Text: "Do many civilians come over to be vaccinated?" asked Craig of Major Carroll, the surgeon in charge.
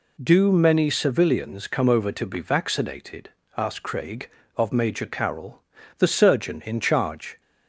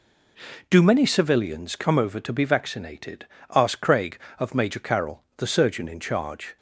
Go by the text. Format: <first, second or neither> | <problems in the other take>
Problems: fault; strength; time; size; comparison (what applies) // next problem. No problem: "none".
neither | none